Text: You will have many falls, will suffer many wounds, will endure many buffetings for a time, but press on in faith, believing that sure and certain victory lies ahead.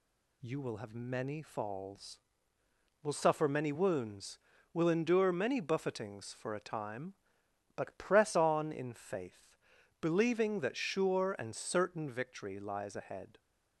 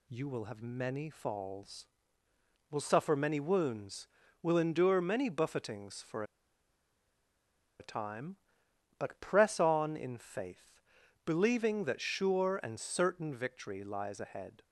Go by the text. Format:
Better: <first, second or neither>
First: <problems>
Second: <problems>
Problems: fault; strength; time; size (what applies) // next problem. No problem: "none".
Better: first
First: none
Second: pauses between "for" and "a"; strong; at 6.2 s; 1.5 s long